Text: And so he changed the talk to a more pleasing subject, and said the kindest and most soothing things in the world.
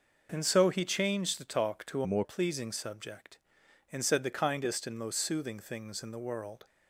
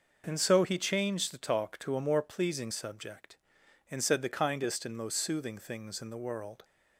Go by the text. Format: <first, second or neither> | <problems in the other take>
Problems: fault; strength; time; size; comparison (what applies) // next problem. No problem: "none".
second | changes voice from "a" to "more"; from 2.0 to 2.2 s; 0.2 s long